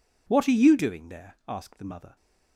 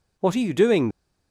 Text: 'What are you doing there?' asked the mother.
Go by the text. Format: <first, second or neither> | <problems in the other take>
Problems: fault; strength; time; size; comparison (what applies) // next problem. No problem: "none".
first | stops before "there asked the mother"; at 0.8 s